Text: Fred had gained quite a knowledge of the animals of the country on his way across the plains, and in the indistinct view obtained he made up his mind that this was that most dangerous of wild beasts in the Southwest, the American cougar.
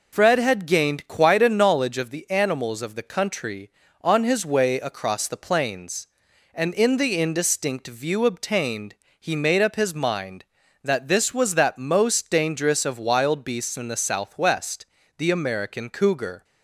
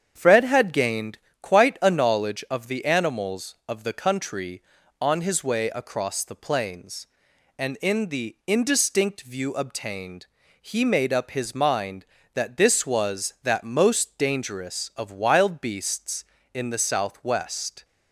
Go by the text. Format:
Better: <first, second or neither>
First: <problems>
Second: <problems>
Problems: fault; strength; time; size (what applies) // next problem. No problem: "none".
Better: first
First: pauses between "obtained" and "he"; slight; at 8.9 s; 0.26 s long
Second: starts louder than the rest; strong; until 1.1 s; 8 dB // pauses between "gained" and "quite"; slight; at 1.1 s; 0.24 s long // pauses between "obtained" and "he"; slight; at 10.2 s; 0.34 s long // stops before "the American cougar"; at 17.8 s